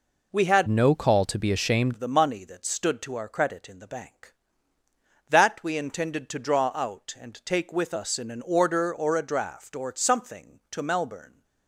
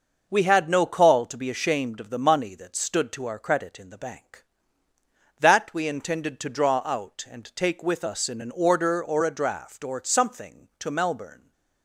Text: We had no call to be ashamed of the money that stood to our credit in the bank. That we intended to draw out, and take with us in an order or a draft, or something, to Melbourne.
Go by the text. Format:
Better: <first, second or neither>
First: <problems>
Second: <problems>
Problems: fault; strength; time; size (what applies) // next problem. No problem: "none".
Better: second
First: changes voice from "no" to "ashamed"; from 0.6 to 1.9 s; 1.3 s long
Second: none